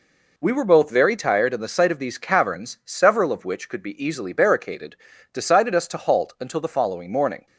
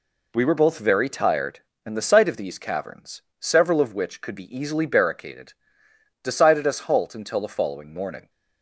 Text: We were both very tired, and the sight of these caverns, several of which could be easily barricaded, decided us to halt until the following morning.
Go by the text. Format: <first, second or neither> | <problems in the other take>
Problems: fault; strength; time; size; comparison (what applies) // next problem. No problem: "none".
first | skips "to"; at 6.7 s